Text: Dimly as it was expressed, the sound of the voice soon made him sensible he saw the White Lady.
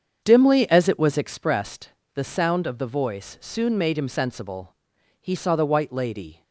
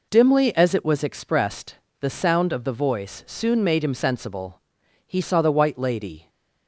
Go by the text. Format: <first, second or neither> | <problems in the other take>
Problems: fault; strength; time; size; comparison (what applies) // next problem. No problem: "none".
second | starts louder than the rest; strong; until 1.6 s; 7.5 dB // pauses between "sensible" and "he"; at 4.7 s; 0.44 s long; also in the second